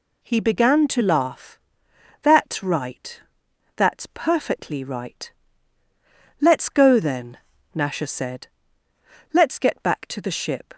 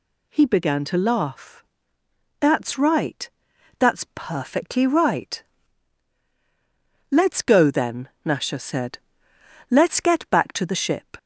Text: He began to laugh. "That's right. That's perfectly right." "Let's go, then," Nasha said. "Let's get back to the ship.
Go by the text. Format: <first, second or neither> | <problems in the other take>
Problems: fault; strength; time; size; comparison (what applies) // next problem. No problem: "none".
neither | none